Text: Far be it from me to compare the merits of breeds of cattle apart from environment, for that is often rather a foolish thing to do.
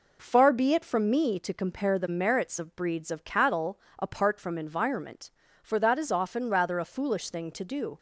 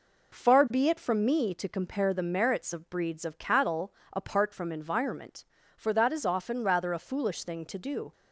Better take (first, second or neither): neither